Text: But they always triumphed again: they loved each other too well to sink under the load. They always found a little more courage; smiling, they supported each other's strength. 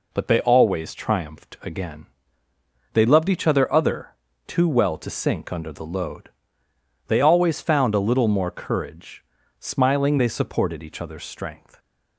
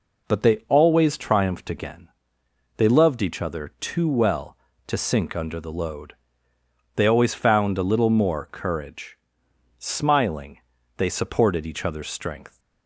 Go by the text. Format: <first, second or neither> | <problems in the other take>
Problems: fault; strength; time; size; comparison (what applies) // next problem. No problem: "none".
second | says "other" twice; at 3.7 s